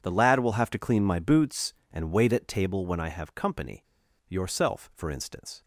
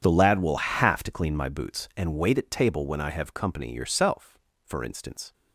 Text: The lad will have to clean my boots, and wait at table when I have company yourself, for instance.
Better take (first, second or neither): second